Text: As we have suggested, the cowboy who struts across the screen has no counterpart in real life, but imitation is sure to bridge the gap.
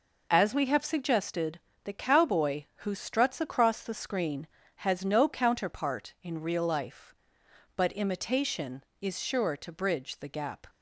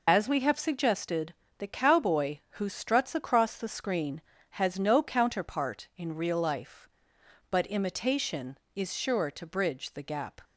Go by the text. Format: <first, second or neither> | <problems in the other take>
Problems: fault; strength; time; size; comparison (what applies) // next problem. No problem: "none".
first | loses the start of "As"; at 0.0 s; 30 ms